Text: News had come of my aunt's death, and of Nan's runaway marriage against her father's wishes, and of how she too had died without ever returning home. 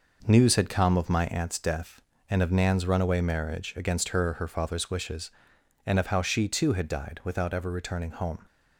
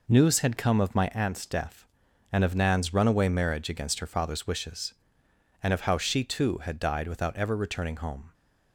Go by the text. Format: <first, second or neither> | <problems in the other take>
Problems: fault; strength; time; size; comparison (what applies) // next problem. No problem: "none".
second | says "her" twice; at 4.3 s